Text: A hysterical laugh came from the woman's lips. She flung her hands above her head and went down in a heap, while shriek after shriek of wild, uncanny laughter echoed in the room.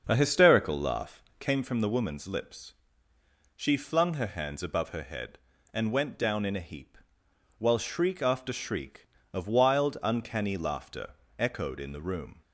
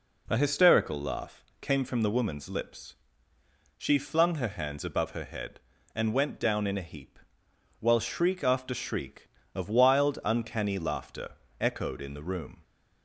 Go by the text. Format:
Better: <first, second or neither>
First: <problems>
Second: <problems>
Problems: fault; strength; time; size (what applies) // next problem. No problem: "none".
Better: second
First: starts louder than the rest; until 1.5 s; 6.5 dB // pauses between "laugh" and "came"; slight; at 1.2 s; 0.16 s long // pauses between "laughter" and "echoed"; slight; at 11.1 s; 0.24 s long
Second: pauses between "laugh" and "came"; slight; at 1.4 s; 0.16 s long // pauses between "laughter" and "echoed"; slight; at 11.3 s; 0.24 s long